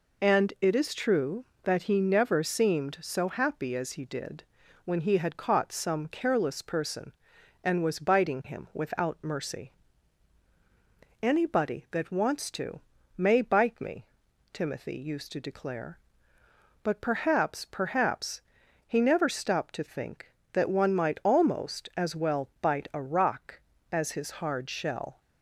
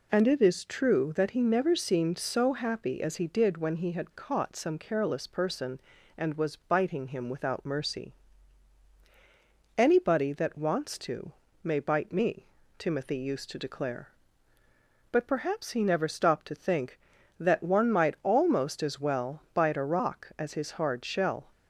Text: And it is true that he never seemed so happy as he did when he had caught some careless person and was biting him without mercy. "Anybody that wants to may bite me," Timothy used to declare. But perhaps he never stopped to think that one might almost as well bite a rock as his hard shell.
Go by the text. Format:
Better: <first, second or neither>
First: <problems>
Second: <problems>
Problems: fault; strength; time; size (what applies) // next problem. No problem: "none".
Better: second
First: pauses between "did" and "when"; at 4.4 s; 0.40 s long // pauses between "to" and "may"; slight; at 12.7 s; 0.36 s long // says "perhaps" twice; at 17.6 s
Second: pauses between "to" and "may"; slight; at 11.3 s; 0.32 s long